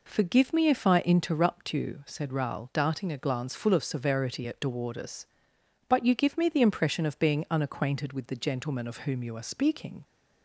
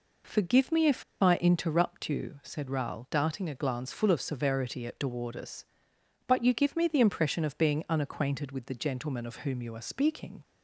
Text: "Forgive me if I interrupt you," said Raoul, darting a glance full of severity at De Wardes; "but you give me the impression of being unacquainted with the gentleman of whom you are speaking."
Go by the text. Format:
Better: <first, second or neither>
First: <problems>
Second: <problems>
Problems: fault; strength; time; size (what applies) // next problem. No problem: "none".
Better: first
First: none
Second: pauses between "if" and "I"; slight; at 1.0 s; 0.19 s long